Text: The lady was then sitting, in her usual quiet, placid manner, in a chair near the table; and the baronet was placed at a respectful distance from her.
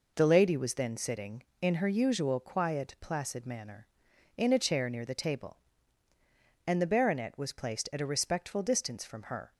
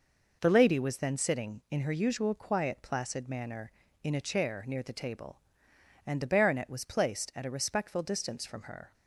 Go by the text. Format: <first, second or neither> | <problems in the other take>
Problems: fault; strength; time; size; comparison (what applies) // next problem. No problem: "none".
neither | none